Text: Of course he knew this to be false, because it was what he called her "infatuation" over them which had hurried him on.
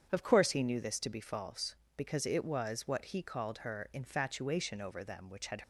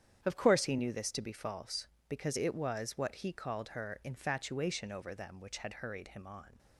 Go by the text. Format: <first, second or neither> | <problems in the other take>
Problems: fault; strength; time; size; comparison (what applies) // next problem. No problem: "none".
second | starts louder than the rest; strong; until 1.1 s; 8 dB; strong in the second // stops before "hurried him on"; at 5.6 s